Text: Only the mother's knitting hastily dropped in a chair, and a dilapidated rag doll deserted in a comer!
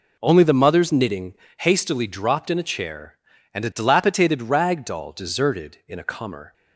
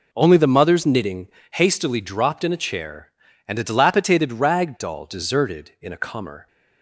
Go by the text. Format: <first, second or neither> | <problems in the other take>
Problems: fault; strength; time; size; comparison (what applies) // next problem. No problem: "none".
neither | pauses between "knitting" and "hastily"; slight; the same in both